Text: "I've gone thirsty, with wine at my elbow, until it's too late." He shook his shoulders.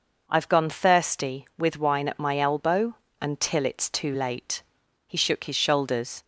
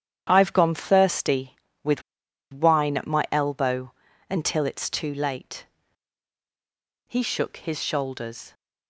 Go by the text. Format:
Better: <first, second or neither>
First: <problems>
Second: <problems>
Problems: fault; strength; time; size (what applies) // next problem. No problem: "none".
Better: first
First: none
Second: starts louder than the rest; strong; until 1.3 s; 9.5 dB // pauses between "with" and "wine"; noticeable; at 2.0 s; 0.49 s long